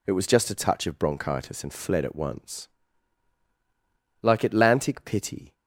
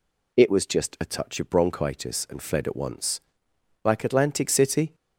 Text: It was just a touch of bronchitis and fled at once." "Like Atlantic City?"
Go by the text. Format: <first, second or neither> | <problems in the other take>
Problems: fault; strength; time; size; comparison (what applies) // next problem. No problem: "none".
second | says "Pity" for "City"; at 5.0 s